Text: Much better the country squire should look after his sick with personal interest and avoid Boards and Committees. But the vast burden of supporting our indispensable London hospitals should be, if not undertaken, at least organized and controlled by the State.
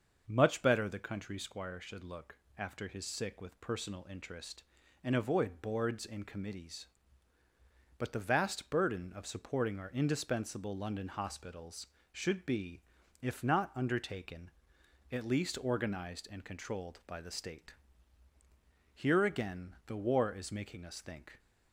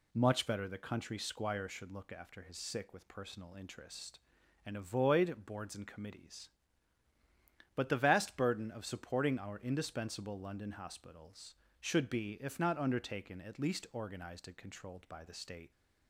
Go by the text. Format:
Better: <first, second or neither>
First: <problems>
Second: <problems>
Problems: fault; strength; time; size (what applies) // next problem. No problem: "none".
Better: second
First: starts louder than the rest; until 1.2 s; 6.5 dB // pauses between "look" and "after"; slight; at 2.3 s; 0.20 s long // goes on to say "Here again the War is making us think"; strong; from 18.9 s on; 2.4 s long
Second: none